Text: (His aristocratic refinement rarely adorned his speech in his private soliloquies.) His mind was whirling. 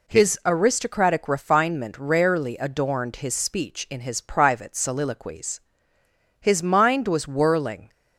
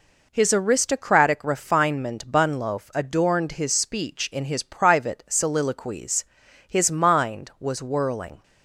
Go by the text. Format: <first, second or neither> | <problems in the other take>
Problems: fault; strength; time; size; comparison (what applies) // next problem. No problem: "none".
first | says "bunloaf" for "rarely"; at 2.3 s